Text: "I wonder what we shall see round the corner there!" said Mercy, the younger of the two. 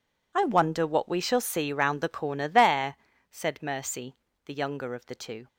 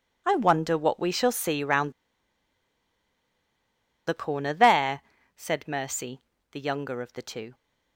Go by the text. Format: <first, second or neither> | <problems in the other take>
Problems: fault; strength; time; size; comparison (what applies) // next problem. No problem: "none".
first | pauses between "round" and "the"; strong; at 1.9 s; 2.1 s long